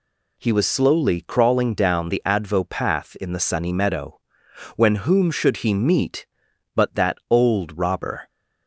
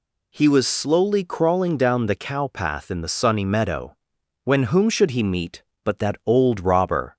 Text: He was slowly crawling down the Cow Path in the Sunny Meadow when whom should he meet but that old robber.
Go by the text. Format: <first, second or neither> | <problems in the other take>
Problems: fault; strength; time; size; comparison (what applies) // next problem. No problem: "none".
second | says "Advo" for "Cow"; at 2.2 s // pauses between "Meadow" and "when"; noticeable; at 4.1 s; 0.62 s long; noticeable in the second